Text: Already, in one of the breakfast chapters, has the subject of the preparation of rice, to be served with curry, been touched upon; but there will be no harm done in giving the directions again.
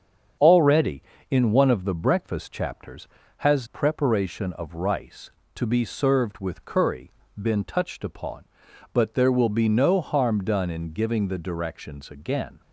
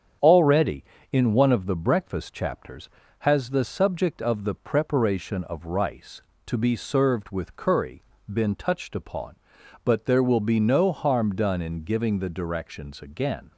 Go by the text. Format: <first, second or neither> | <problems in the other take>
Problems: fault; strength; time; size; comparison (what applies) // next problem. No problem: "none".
second | starts louder than the rest; strong; until 1.7 s; 7.5 dB; strong in the second // skips "the subject of the"; at 3.6 s